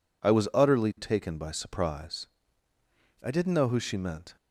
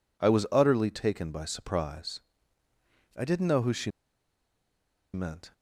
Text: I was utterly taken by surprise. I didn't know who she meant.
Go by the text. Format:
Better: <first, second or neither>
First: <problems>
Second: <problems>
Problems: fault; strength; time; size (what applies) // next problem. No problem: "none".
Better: first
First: none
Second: pauses between "she" and "meant"; at 3.8 s; 1.2 s long